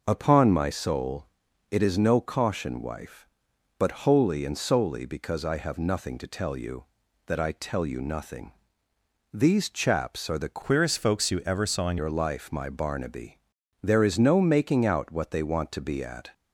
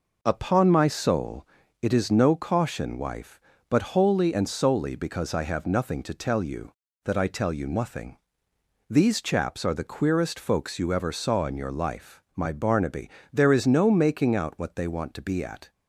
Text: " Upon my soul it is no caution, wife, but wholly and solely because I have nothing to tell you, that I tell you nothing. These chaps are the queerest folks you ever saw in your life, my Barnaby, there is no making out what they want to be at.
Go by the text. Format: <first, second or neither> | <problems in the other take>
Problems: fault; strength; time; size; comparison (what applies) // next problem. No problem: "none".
second | pauses between "soul" and "it"; at 1.2 s; 0.42 s long; slight in the second // changes voice from "queerest" to "in"; from 10.6 to 11.9 s; 1.3 s long